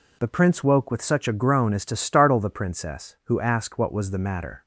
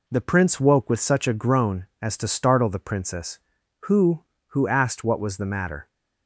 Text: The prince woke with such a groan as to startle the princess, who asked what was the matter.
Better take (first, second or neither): first